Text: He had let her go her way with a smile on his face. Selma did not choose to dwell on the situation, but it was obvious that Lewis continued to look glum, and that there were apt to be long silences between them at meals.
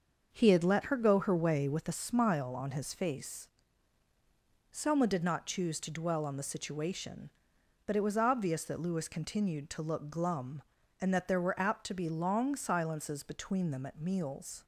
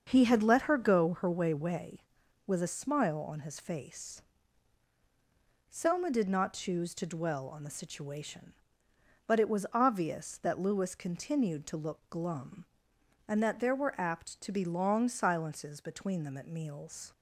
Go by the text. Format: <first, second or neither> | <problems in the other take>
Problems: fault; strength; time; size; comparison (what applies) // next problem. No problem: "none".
first | starts louder than the rest; until 1.0 s; 6.5 dB; also in the first // says "way" twice; at 1.5 s